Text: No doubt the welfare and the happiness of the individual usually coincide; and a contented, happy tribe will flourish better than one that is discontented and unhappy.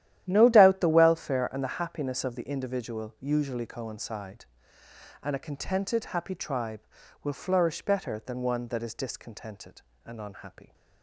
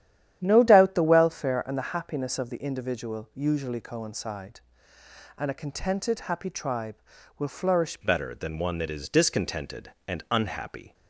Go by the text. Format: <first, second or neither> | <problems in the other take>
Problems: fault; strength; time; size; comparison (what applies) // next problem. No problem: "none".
first | starts louder than the rest; strong; until 1.4 s; 10.5 dB; strong in the first // changes voice at "better"; from 8.0 s on; 2.9 s long